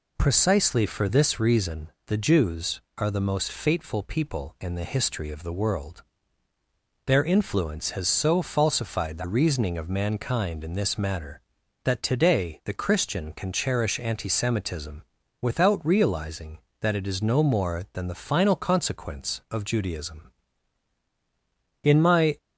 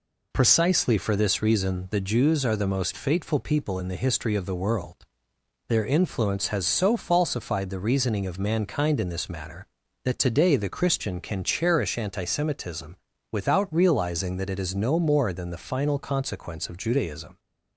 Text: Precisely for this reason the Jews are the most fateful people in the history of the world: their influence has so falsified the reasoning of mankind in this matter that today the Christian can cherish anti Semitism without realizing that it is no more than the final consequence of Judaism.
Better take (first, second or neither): second